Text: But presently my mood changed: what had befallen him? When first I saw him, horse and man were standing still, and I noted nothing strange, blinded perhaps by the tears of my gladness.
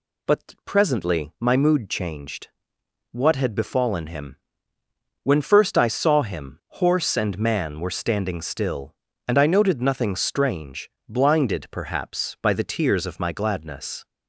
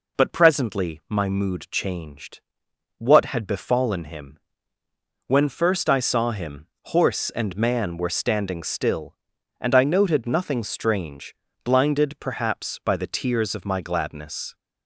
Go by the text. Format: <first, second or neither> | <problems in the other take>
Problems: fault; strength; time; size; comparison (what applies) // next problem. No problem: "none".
neither | none